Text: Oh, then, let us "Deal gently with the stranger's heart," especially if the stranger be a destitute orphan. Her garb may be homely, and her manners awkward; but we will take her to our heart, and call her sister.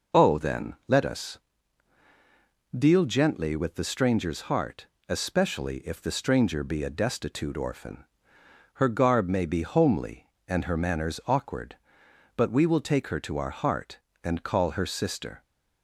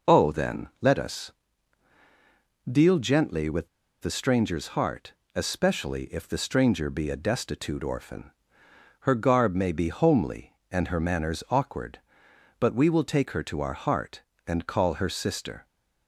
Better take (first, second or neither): first